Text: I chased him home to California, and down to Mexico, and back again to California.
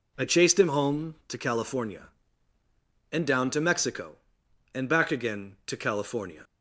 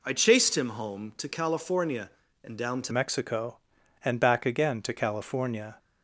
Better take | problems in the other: first | changes voice at "Mexico"; from 2.9 s on; 2.8 s long

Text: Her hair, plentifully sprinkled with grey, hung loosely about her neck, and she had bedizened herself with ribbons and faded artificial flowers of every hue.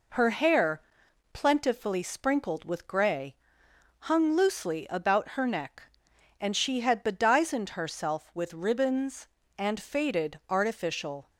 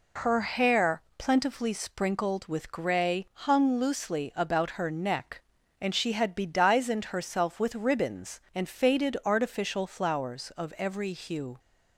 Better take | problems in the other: second | stops before "flowers of every hue"; at 11.2 s

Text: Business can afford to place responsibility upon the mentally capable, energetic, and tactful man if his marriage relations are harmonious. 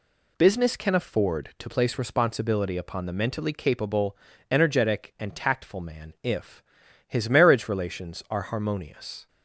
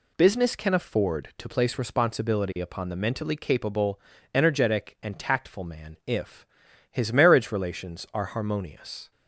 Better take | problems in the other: neither | pauses between "if" and "his"; the same in both

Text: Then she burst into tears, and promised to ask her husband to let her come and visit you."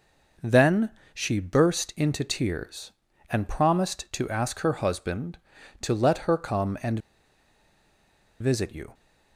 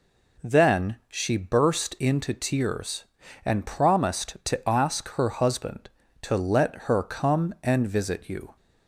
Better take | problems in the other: second | pauses between "Then" and "she"; slight; at 0.8 s; 0.24 s long // pauses between "and" and "visit"; strong; at 6.9 s; 1.4 s long

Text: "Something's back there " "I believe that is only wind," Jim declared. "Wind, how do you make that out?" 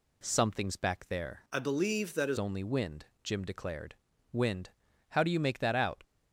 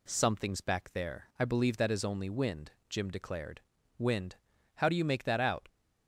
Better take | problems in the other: second | changes voice from "I" to "is"; from 1.5 to 2.3 s; 0.8 s long

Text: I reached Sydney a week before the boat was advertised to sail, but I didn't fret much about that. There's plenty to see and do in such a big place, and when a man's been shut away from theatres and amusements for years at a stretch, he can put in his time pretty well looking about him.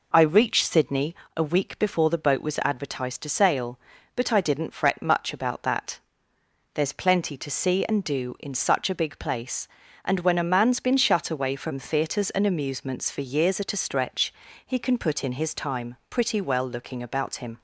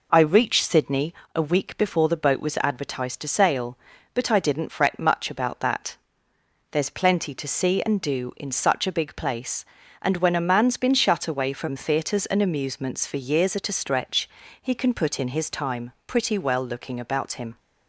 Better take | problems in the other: neither | pauses between "Sydney" and "a"; slight; the same in both

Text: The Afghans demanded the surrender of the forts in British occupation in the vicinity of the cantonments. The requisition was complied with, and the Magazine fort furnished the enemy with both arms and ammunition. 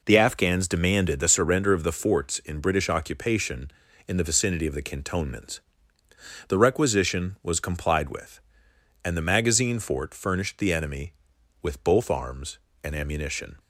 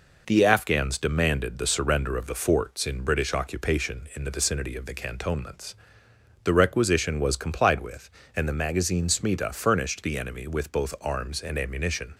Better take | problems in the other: first | says "smita" for "fort"; at 9.0 s

